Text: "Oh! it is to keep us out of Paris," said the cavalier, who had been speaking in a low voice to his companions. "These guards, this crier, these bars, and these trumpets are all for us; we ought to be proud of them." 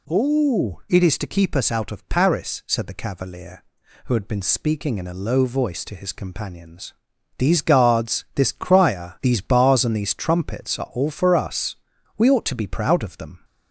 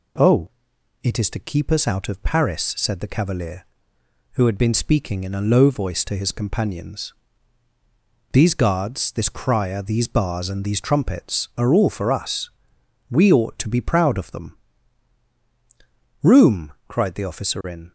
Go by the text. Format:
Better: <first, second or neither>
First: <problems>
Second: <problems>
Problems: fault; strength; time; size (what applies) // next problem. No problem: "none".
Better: first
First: none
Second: goes on to say "Room cried the officer in"; strong; from 16.2 s on; 1.6 s long